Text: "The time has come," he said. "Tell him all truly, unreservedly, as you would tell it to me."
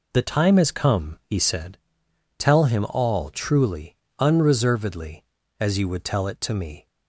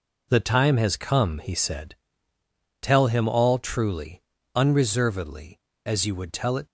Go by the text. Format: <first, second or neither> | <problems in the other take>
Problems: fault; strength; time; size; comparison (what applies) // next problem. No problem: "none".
first | stops before "to me"; at 6.6 s